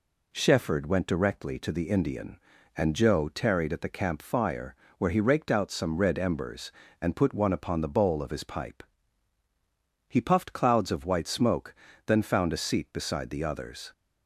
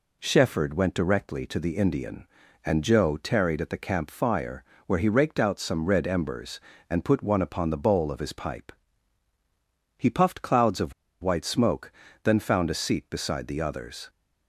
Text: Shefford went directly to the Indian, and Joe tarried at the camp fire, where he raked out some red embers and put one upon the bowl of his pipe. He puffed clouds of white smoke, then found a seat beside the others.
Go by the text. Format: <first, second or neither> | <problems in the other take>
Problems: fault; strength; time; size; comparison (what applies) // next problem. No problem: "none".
first | pauses between "of" and "white"; slight; at 10.9 s; 0.30 s long